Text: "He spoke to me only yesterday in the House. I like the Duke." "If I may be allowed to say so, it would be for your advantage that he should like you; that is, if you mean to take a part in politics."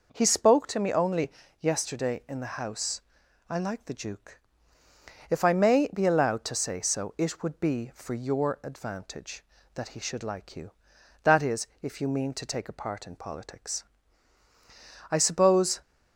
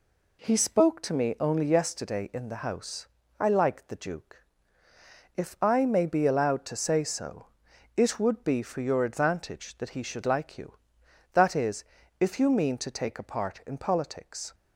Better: second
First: pauses between "only" and "yesterday"; slight; at 1.3 s; 0.30 s long // goes on to say "I suppose"; noticeable; from 15.1 s on; 0.66 s long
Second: none

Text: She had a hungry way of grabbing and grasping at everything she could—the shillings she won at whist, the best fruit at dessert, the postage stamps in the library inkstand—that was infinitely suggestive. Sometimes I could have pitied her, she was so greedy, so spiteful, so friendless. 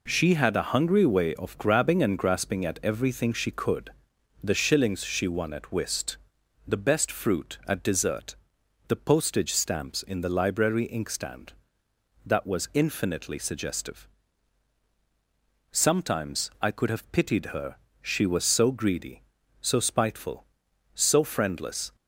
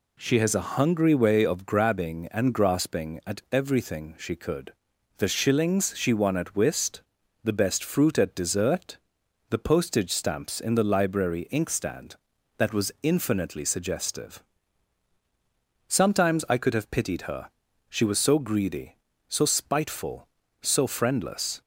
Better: first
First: none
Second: says "has" for "had"; at 0.3 s

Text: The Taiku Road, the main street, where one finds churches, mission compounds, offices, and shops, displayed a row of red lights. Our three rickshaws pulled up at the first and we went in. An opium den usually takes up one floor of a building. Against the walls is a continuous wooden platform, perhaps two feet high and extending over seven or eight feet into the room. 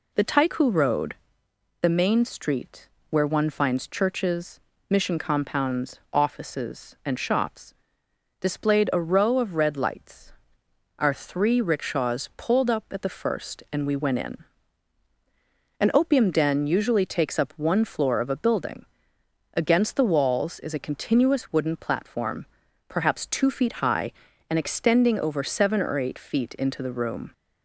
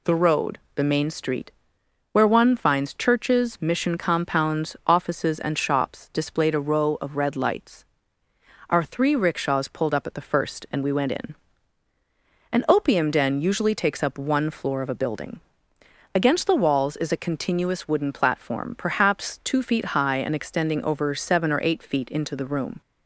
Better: first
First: none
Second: skips "Taiku"; at 0.1 s

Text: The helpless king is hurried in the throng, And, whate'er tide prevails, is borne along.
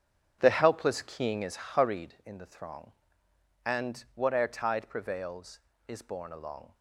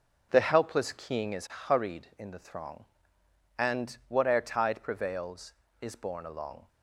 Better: second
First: starts louder than the rest; strong; until 2.1 s; 8 dB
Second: none

